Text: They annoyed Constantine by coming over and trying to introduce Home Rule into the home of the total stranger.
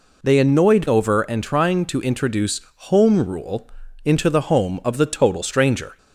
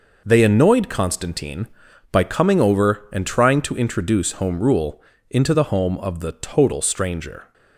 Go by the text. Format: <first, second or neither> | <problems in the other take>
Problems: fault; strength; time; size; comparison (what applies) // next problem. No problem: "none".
second | skips "Constantine by coming"; at 0.8 s // pauses between "introduce" and "Home"; slight; at 2.6 s; 0.26 s long // pauses between "Rule" and "into"; slight; at 3.6 s; 0.34 s long; slight in the second